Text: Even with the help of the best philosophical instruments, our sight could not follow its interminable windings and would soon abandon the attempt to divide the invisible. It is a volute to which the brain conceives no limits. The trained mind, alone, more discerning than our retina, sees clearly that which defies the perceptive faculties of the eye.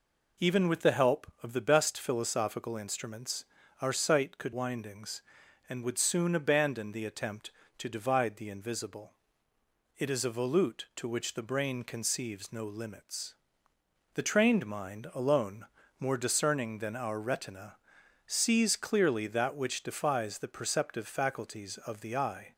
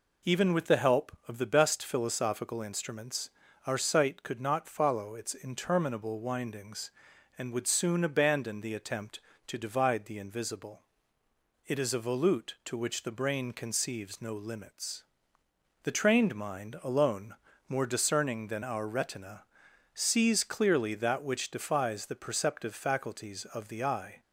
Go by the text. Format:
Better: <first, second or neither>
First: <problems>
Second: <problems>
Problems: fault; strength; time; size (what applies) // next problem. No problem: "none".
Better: second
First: skips "not follow its interminable"; at 4.5 s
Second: none